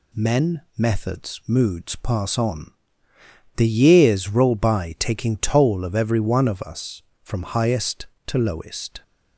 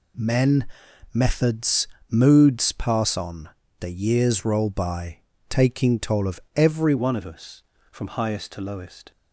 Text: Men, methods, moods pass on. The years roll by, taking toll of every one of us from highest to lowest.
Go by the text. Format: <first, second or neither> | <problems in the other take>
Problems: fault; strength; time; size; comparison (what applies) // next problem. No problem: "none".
first | pauses between "of" and "every"; slight; at 6.3 s; 0.16 s long // changes voice at "one"; from 6.9 s on; 2.2 s long